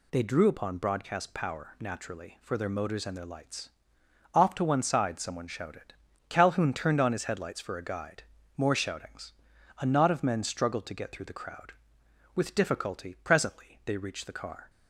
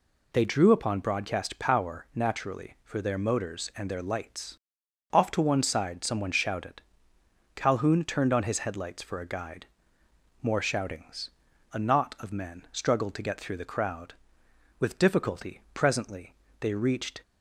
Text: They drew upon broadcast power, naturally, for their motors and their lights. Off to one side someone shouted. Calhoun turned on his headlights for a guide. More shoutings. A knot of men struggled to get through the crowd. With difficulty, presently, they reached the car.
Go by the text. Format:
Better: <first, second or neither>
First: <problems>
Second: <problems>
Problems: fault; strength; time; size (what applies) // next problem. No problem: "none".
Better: first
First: none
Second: stops before "the car"; at 17.2 s